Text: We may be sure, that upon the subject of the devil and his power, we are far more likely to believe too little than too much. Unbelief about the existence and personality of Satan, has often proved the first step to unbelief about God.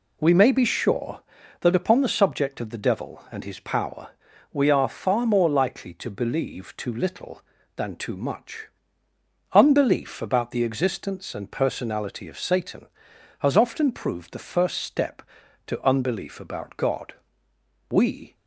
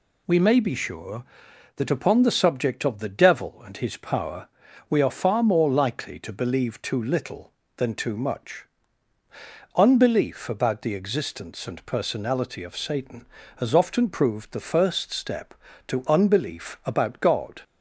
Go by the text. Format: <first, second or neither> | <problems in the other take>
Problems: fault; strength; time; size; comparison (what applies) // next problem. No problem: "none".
second | goes on to say "We"; slight; from 17.8 s on; 0.46 s long